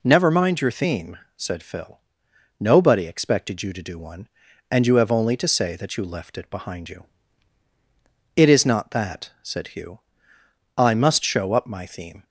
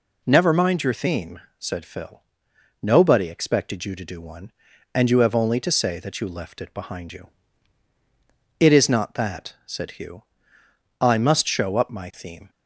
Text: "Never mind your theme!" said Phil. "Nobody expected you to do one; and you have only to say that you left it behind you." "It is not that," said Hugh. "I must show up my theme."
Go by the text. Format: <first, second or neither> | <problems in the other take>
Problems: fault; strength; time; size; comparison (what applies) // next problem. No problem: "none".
neither | none